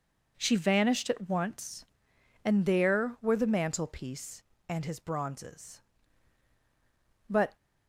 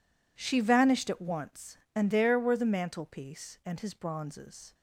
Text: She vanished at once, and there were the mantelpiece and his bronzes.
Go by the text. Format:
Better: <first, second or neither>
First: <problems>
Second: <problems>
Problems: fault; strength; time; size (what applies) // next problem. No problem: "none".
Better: second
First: goes on to say "But"; slight; from 7.2 s on; 0.28 s long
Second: none